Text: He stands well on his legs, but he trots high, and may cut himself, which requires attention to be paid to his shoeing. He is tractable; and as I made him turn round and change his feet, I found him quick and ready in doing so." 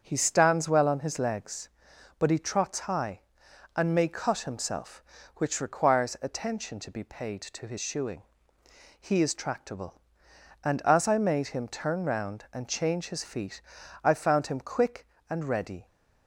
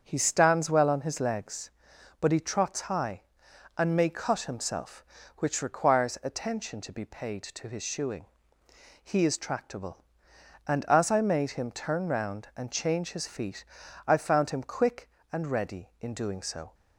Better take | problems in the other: second | starts louder than the rest; strong; until 1.0 s; 7 dB; strong in the second // stops before "in doing so"; at 15.8 s

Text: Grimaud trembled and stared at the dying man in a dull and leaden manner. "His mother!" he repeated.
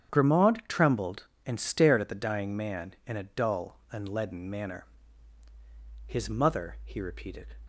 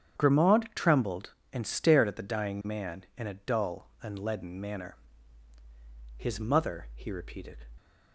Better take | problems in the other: neither | starts louder than the rest; strong; the same in both

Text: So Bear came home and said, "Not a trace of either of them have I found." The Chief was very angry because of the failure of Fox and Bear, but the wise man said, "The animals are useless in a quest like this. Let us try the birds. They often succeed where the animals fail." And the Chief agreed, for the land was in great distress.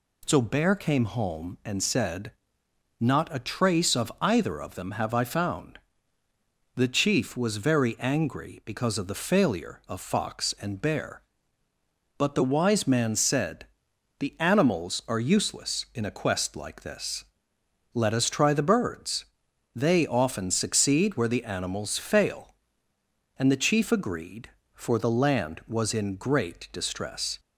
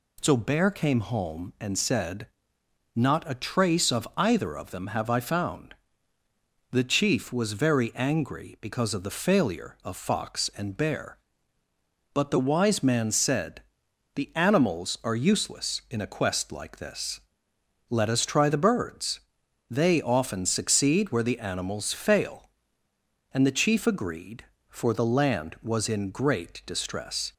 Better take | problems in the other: neither | none

